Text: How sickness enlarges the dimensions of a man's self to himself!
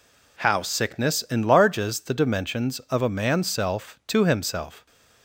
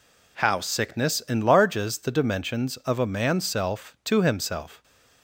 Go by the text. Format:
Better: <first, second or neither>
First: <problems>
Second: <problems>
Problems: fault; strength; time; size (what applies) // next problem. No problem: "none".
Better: neither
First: none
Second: none